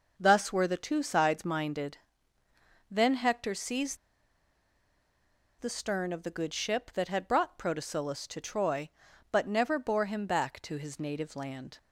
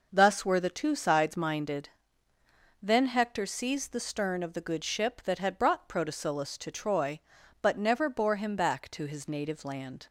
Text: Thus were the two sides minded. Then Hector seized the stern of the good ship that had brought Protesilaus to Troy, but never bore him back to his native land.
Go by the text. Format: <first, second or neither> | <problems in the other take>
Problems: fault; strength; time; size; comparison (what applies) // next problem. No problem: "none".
second | pauses between "seized" and "the"; strong; at 3.9 s; 1.6 s long